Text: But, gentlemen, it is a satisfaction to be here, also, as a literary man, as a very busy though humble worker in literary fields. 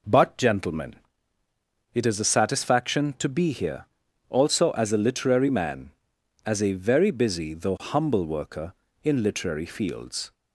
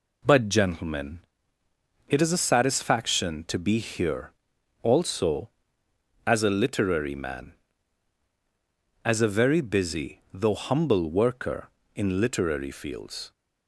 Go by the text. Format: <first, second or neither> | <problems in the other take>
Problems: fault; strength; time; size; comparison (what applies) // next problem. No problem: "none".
neither | none